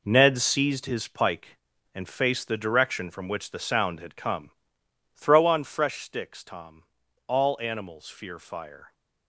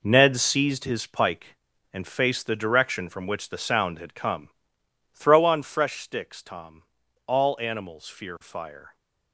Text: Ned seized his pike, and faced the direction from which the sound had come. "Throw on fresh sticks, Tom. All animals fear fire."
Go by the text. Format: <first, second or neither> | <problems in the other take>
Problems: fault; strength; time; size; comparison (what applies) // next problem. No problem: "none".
neither | none